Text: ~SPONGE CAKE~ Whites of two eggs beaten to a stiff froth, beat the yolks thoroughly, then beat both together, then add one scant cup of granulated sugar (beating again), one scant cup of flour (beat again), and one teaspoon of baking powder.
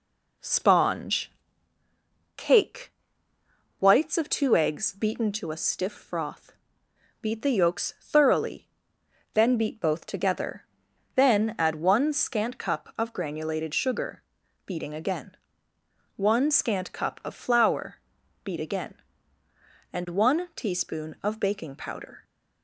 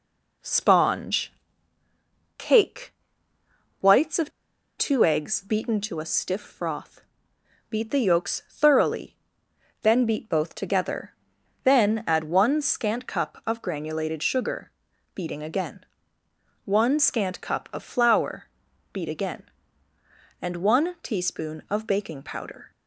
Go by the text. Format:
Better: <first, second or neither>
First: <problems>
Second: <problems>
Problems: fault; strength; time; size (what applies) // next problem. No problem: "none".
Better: first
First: pauses between "SPONGE" and "CAKE"; at 1.3 s; 1.0 s long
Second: pauses between "SPONGE" and "CAKE"; at 1.3 s; 1.0 s long // pauses between "of" and "two"; noticeable; at 4.3 s; 0.47 s long